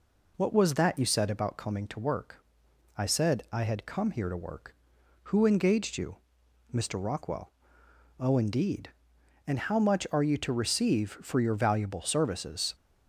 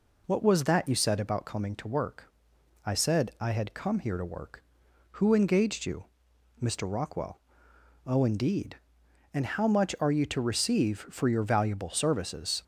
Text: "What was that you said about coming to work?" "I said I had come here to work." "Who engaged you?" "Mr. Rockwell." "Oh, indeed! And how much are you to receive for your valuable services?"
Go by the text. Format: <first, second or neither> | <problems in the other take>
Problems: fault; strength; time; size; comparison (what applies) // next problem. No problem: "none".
neither | none